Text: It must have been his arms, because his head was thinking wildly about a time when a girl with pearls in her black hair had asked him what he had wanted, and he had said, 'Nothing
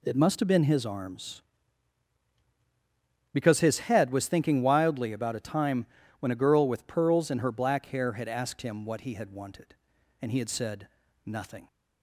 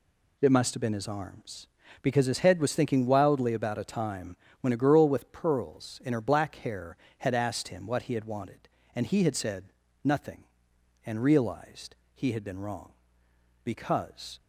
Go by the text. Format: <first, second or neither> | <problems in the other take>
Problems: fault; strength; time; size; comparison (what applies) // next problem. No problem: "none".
first | pauses between "time" and "when"; slight; at 4.3 s; 0.24 s long; slight in the first // goes on to say "and realized he had been wrong because"; strong; from 11.0 s on; 3.3 s long